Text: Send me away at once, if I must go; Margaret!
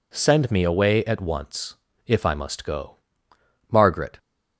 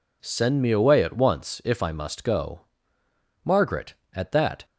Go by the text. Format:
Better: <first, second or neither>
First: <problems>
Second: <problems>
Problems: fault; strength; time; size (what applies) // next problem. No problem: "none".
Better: first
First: none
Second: goes on to say "At that"; from 4.1 s on; 0.52 s long